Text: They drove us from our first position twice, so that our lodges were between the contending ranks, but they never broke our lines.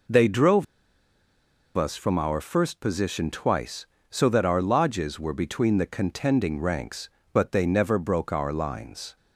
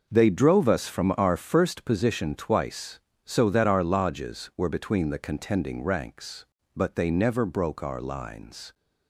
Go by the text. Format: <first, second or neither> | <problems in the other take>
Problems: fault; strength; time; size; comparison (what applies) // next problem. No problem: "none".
second | pauses between "drove" and "us"; at 0.6 s; 1.1 s long